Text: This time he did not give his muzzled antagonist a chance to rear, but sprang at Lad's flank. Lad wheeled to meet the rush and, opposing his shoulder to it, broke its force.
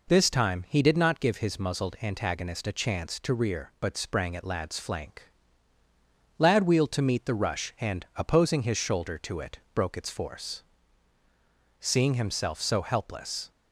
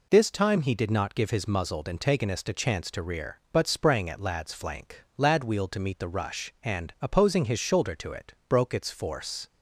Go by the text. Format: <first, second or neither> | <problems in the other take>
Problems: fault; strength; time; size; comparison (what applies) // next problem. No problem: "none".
second | goes on to say "Seeing himself so helpless"; strong; from 11.8 s on; 1.7 s long